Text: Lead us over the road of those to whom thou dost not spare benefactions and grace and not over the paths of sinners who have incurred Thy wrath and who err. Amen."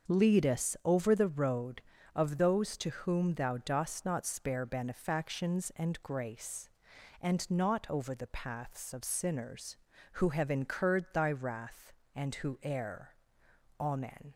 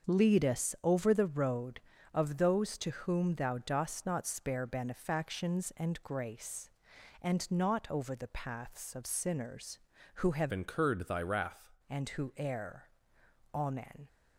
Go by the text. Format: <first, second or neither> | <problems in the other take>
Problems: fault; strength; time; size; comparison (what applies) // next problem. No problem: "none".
first | starts louder than the rest; until 1.1 s; 6.5 dB; also in the first // changes voice from "incurred" to "wrath"; from 10.5 to 11.6 s; 1.1 s long